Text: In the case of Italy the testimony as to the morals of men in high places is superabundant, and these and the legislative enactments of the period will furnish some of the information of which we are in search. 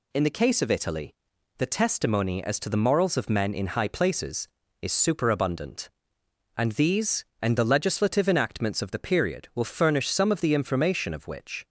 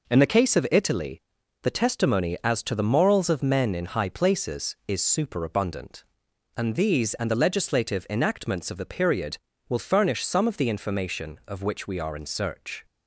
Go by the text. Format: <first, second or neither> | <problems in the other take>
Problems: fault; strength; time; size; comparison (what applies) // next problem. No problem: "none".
second | pauses between "Italy" and "the"; at 1.1 s; 0.42 s long; also in the second // stops before "we are in search"; at 11.6 s